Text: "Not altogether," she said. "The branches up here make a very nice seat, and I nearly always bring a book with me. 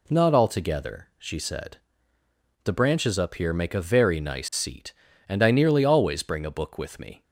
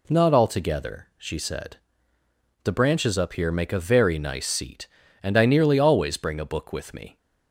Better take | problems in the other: neither | none

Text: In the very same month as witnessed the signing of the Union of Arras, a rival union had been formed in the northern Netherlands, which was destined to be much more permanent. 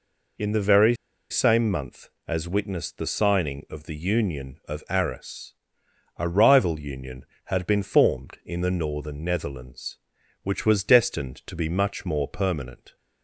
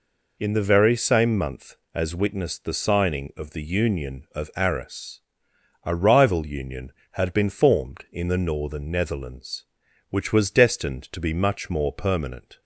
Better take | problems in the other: second | pauses between "very" and "same"; slight; at 0.9 s; 0.36 s long

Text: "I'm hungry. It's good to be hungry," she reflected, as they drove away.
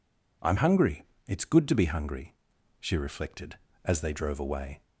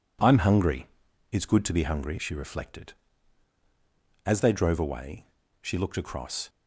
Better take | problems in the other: first | goes on to say "She looked across"; noticeable; from 5.6 s on; 0.88 s long

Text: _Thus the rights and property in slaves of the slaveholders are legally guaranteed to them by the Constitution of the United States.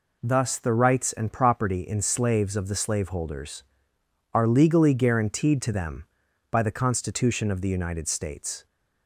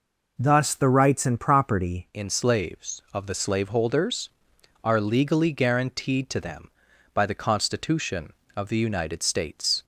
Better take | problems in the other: first | changes voice at "in"; from 2.1 s on; 7.7 s long

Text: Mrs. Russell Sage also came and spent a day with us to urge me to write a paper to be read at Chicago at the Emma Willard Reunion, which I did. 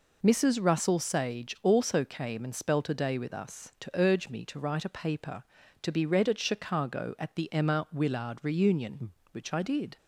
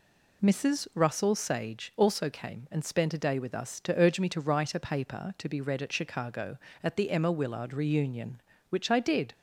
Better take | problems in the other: second | says "spelt" for "spent"; at 2.5 s

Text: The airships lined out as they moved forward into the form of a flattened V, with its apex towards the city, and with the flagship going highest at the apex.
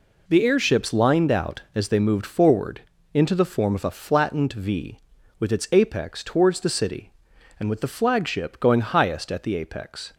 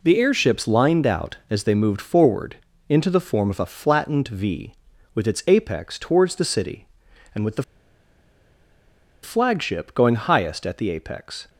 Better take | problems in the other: first | pauses between "forward" and "into"; slight; at 2.5 s; 0.32 s long; slight in the first // pauses between "the" and "flagship"; strong; at 7.6 s; 1.6 s long

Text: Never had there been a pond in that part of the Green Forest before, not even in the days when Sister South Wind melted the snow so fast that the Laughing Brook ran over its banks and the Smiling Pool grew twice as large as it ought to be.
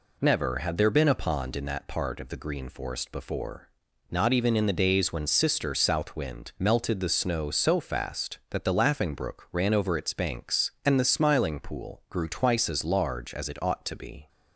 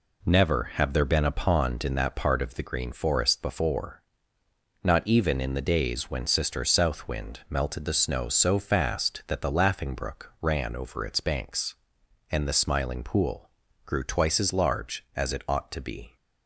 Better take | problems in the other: first | says "have" for "had"; at 0.7 s // pauses between "Pool" and "grew"; slight; at 13.4 s; 0.34 s long

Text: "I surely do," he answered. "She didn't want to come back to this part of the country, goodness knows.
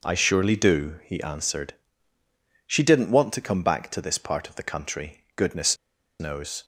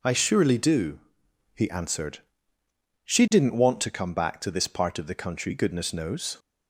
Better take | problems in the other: second | pauses between "goodness" and "knows"; at 5.7 s; 0.44 s long

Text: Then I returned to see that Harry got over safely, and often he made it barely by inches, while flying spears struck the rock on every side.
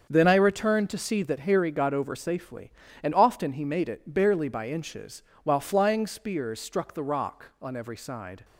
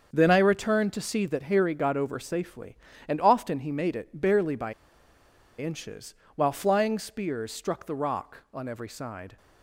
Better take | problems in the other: first | starts louder than the rest; until 1.1 s; 7 dB; also in the first // pauses between "by" and "inches"; noticeable; at 4.7 s; 0.87 s long

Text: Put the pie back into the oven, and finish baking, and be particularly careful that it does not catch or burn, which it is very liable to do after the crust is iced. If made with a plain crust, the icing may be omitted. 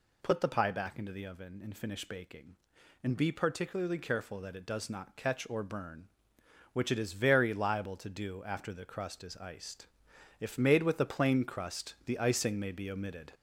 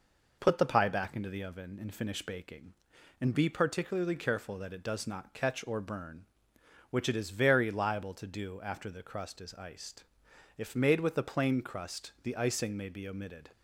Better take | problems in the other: second | gets louder; noticeable; throughout; 5 dB

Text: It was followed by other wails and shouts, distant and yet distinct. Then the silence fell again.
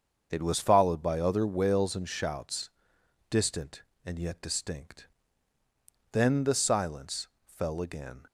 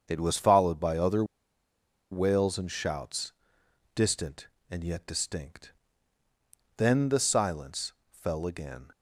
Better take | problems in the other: first | starts louder than the rest; until 1.0 s; 7 dB; also in the first // pauses between "other" and "wails"; noticeable; at 1.2 s; 0.87 s long // pauses between "silence" and "fell"; slight; at 7.9 s; 0.18 s long; slight in the first

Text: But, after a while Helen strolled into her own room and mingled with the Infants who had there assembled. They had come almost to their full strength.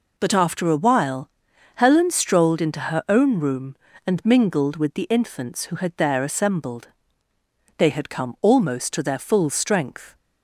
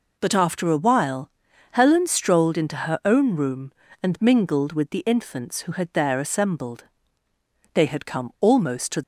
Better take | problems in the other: first | pauses between "while" and "Helen"; at 1.2 s; 0.42 s long; noticeable in the first // stops before "their full strength"; at 9.0 s

